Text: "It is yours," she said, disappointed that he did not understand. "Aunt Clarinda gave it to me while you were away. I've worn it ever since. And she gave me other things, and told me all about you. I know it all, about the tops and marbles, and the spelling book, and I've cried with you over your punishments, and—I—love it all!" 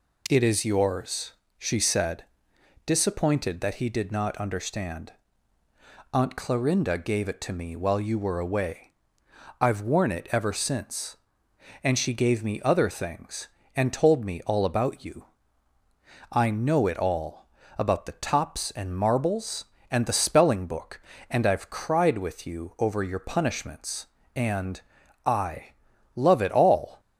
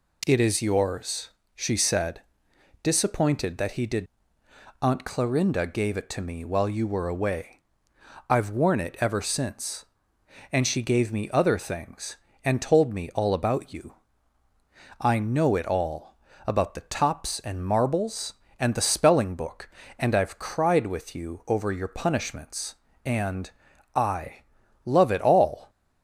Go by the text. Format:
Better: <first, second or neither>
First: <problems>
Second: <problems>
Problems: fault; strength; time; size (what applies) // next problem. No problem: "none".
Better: first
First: none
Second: skips "not understand"; at 4.4 s